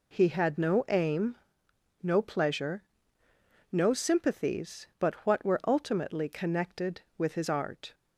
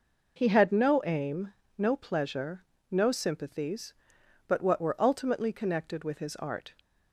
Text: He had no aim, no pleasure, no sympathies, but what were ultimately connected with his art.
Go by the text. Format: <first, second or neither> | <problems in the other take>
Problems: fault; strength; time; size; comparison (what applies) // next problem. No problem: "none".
neither | none